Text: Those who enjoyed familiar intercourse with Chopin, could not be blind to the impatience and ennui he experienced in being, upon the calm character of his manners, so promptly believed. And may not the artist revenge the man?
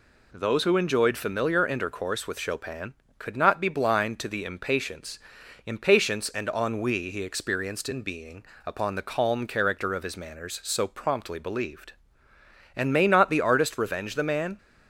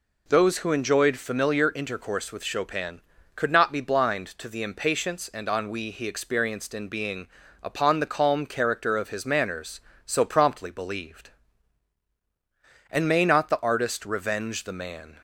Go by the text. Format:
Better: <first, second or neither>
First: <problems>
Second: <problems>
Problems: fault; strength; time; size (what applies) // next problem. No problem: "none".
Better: second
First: says "impatience" twice; at 5.6 s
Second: none